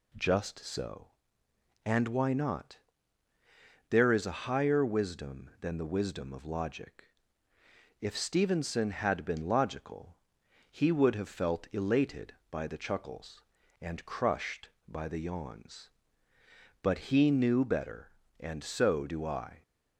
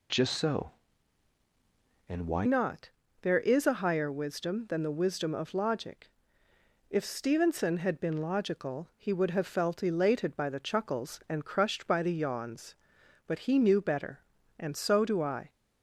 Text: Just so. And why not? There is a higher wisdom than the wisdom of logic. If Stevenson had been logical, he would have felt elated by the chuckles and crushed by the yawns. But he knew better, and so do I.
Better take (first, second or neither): first